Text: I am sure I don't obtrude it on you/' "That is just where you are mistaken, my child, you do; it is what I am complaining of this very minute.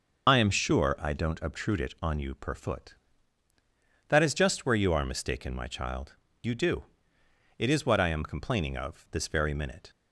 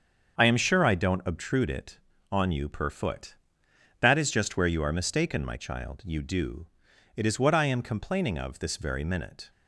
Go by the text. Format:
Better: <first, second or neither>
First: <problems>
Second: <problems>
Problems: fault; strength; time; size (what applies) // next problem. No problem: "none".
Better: second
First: loses the start of "I"; at 0.2 s; 55 ms // starts louder than the rest; noticeable; until 1.3 s; 6 dB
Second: starts louder than the rest; until 1.3 s; 7 dB